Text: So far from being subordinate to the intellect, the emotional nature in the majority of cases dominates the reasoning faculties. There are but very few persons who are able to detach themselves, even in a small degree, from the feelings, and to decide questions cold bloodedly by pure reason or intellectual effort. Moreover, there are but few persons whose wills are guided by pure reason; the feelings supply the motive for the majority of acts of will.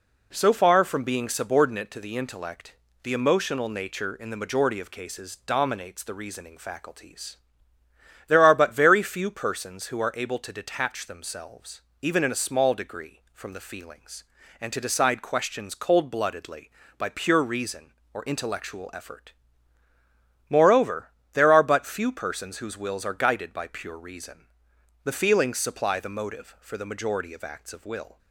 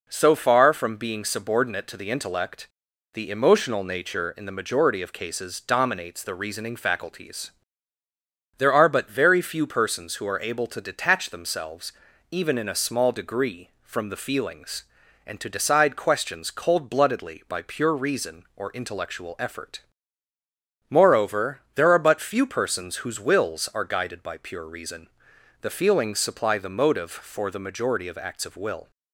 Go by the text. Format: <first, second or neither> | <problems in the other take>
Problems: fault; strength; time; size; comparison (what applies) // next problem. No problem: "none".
neither | none